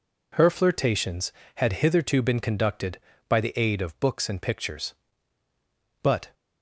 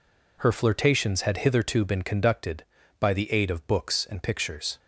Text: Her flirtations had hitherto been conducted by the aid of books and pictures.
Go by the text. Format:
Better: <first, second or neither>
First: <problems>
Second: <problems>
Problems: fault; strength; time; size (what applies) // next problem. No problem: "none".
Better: second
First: goes on to say "But"; slight; from 6.0 s on; 0.32 s long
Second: none